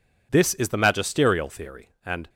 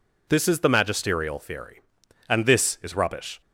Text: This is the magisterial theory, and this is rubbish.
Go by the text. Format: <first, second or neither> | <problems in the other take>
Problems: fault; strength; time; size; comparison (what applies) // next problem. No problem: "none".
second | stops before "this is rubbish"; at 2.2 s